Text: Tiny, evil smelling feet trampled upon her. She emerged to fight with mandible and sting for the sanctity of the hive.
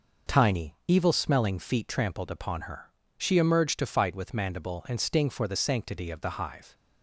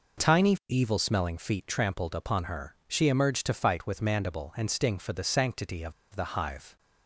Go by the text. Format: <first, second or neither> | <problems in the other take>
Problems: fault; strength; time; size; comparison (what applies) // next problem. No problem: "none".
first | pauses between "of" and "the"; slight; at 5.9 s; 0.21 s long